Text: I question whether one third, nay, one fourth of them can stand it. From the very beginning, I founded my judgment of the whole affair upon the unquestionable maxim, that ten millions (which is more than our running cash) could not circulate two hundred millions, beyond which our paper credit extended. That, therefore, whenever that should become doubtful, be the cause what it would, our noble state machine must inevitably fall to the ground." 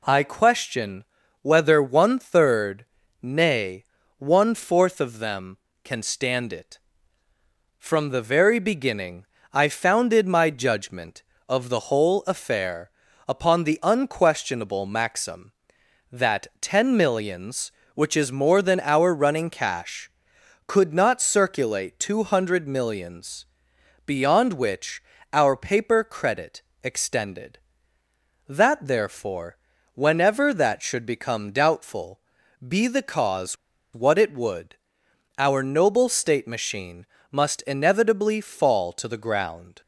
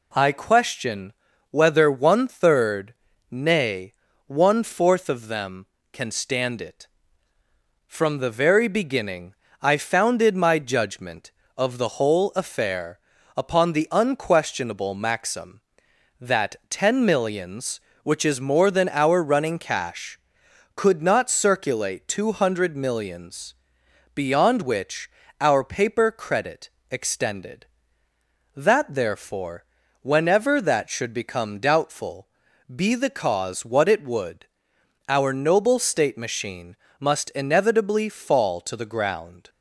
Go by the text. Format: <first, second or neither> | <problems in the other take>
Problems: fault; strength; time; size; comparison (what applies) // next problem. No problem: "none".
second | pauses between "question" and "whether"; at 1.0 s; 0.38 s long; also in the second // pauses between "affair" and "upon"; at 12.8 s; 0.40 s long; also in the second // pauses between "which" and "our"; slight; at 25.0 s; 0.30 s long; slight in the second // pauses between "credit" and "extended"; slight; at 26.6 s; 0.22 s long; slight in the second // pauses between "cause" and "what"; at 33.5 s; 0.38 s long // pauses between "machine" and "must"; slight; at 37.0 s; 0.28 s long; slight in the second